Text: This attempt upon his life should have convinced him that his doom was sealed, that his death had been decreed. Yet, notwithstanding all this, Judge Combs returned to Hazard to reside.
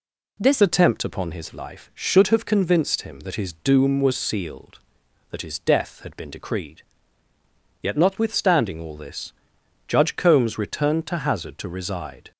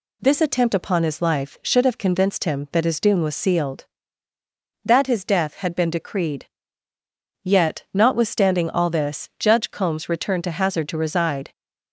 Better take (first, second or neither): second